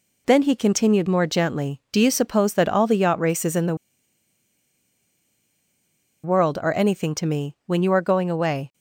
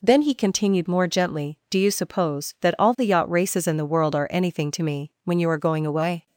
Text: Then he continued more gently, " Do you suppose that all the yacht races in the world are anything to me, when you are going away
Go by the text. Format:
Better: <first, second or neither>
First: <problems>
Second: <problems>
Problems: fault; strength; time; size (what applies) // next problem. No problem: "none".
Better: second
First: pauses between "the" and "world"; strong; at 3.7 s; 2.4 s long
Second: none